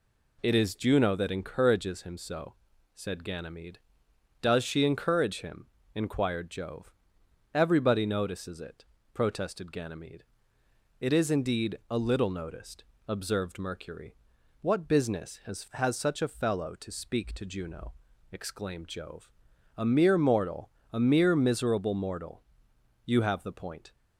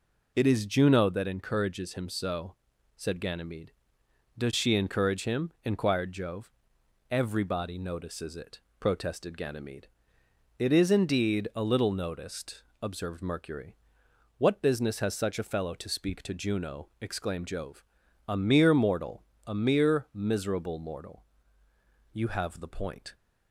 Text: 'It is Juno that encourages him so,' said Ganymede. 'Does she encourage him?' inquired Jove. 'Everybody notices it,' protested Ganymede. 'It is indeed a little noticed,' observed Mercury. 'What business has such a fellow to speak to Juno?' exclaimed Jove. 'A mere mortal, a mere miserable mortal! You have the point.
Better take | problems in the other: second | says "has" twice; at 15.7 s

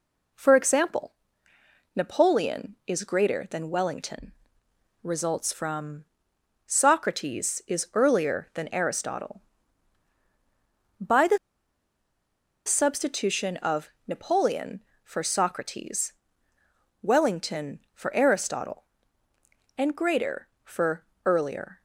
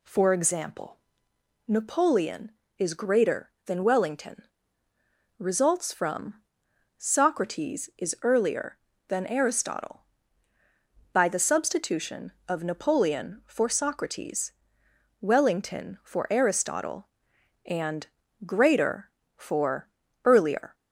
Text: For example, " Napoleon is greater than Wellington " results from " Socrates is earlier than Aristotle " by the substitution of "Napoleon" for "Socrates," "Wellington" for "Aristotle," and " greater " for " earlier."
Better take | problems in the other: second | pauses between "the" and "substitution"; strong; at 11.3 s; 1.2 s long // pauses between "of" and "Napoleon"; slight; at 13.9 s; 0.18 s long

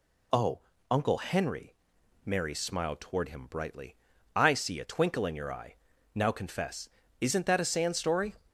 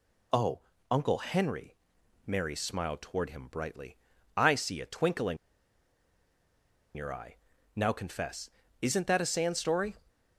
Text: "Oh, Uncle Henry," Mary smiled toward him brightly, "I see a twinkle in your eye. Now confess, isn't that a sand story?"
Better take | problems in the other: first | pauses between "in" and "your"; strong; at 5.3 s; 1.5 s long

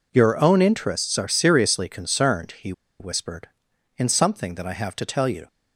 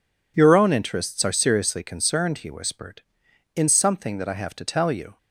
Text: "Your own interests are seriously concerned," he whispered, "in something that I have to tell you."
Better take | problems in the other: second | pauses between "he" and "whispered"; slight; at 2.7 s; 0.28 s long

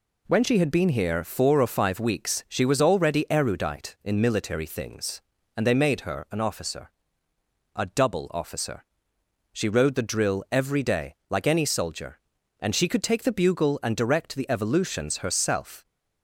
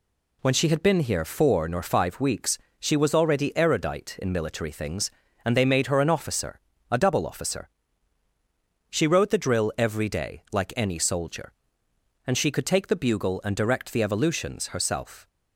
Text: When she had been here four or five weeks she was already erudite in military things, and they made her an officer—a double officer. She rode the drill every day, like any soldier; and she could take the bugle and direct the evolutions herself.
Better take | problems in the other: first | says "nor" for "or"; at 1.6 s // pauses between "weeks" and "she"; slight; at 2.5 s; 0.22 s long

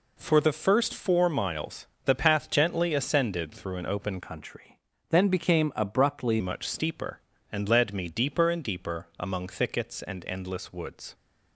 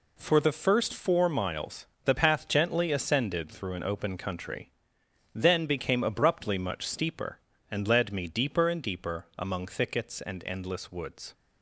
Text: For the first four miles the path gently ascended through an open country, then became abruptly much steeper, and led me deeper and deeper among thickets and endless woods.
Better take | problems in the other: second | pauses between "miles" and "the"; slight; at 1.8 s; 0.20 s long; slight in the second // changes voice from "country" to "abruptly"; from 4.2 to 6.4 s; 2.2 s long

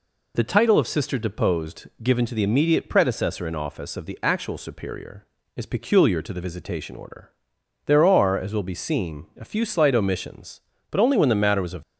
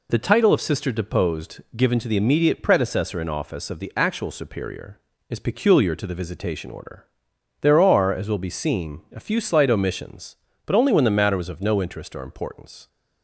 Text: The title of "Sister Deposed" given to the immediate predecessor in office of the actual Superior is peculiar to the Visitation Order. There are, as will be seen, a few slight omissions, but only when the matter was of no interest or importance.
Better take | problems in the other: second | stops before "no interest or importance"; at 11.8 s

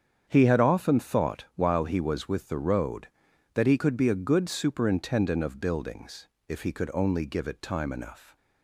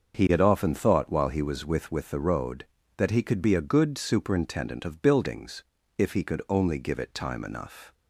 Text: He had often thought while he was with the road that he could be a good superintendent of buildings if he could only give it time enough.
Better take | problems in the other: first | starts louder than the rest; until 1.2 s; 6.5 dB; strong in the first // says "with" twice; at 1.9 s // pauses between "buildings" and "if"; slight; at 5.6 s; 0.36 s long; slight in the first

